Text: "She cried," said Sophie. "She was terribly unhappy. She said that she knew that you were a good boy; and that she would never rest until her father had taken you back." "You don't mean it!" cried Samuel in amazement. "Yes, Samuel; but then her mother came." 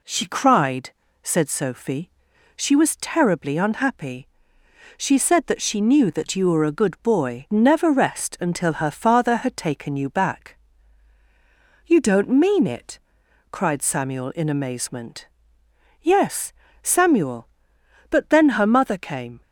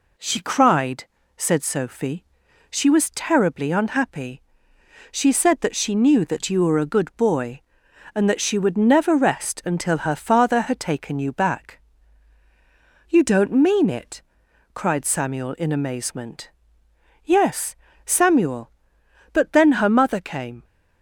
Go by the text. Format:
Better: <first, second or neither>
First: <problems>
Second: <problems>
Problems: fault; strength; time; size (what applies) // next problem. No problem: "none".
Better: second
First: skips "and that she would"; at 7.4 s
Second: none